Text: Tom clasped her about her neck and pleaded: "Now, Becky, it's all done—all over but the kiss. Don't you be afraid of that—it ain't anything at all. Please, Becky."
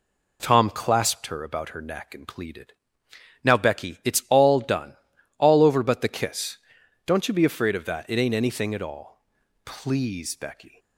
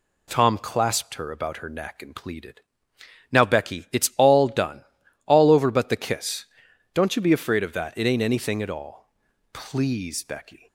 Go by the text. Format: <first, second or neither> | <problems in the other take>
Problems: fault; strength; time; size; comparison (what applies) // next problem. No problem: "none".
second | starts louder than the rest; slight; until 1.4 s; 3 dB